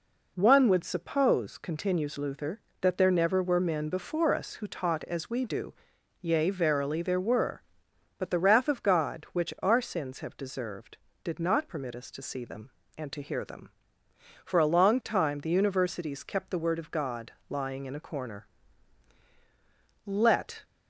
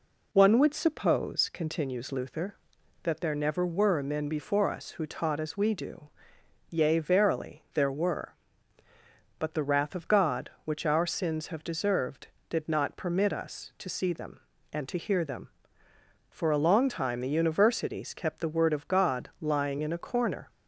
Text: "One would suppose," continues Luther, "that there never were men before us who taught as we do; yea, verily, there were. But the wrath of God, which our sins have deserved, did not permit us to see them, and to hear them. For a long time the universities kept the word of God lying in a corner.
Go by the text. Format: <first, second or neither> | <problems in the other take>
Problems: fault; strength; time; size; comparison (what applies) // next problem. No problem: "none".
second | pauses between "God" and "lying"; slight; at 17.3 s; 0.16 s long // goes on to say "Let"; from 20.0 s on; 0.58 s long